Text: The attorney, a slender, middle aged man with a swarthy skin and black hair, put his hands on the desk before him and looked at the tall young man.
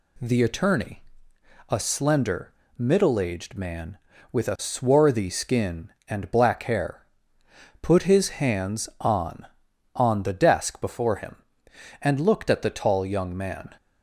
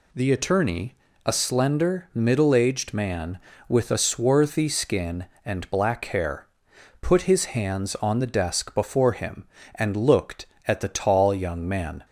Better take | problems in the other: second | says "on" twice; at 9.9 s

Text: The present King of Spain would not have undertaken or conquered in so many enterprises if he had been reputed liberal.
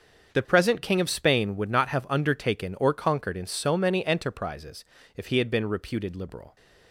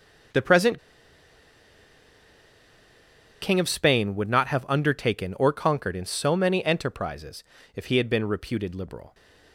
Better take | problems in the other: first | starts louder than the rest; until 3.9 s; 7 dB; also in the first // pauses between "present" and "King"; strong; at 0.7 s; 2.6 s long // pauses between "enterprises" and "if"; slight; at 7.4 s; 0.32 s long; slight in the first

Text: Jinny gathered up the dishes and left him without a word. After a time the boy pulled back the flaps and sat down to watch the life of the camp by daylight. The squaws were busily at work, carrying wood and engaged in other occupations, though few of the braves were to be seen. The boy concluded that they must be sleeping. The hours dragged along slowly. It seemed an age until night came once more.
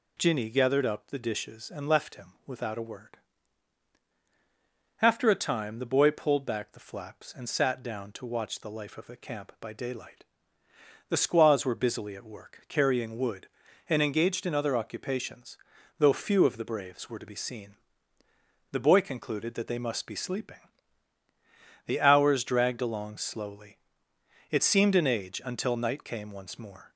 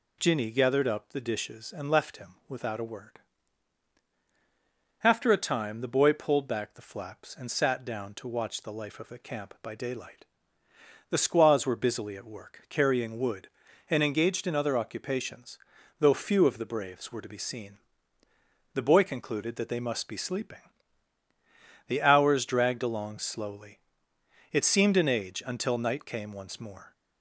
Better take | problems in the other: neither | none

